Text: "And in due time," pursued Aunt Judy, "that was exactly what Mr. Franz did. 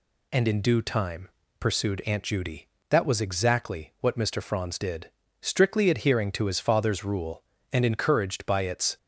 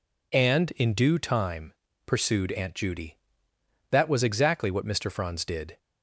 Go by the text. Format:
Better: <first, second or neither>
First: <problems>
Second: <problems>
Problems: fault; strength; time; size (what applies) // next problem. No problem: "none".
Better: second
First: goes on to say "Strictly adhering to his father's rule and encouraged by its"; strong; from 5.3 s on; 3.5 s long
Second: none